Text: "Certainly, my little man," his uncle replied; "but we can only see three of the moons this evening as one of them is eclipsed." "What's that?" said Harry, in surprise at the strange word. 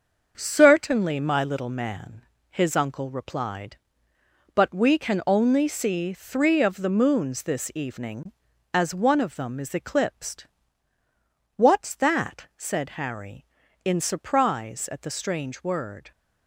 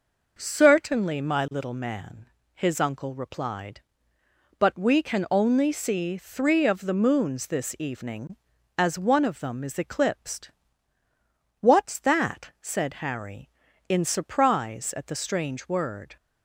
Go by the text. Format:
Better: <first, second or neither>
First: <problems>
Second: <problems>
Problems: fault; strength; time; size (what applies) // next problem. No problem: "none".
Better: second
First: gets quieter; throughout; 7 dB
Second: none